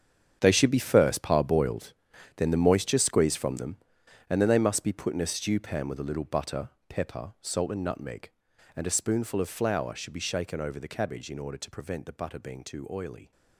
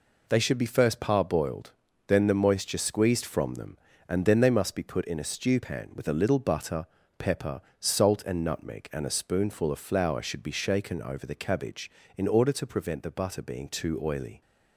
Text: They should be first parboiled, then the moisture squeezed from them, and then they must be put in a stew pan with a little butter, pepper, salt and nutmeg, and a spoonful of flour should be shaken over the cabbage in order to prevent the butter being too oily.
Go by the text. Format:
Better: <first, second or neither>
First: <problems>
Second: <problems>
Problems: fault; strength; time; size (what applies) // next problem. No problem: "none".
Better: second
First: gets quieter; strong; throughout; 14 dB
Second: none